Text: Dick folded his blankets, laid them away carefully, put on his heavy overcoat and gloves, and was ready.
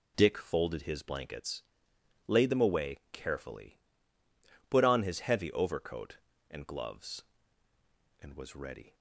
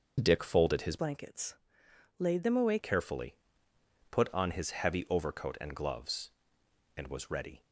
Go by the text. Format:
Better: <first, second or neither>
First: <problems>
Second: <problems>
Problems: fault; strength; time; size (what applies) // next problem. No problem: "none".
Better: first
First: none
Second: changes voice from "blankets" to "away"; from 0.9 to 2.7 s; 1.8 s long